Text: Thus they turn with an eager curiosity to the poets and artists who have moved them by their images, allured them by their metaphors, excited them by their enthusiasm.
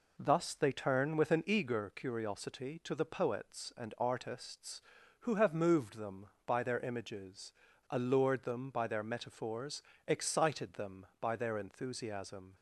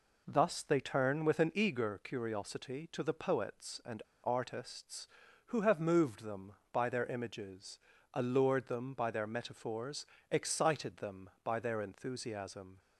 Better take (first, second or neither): first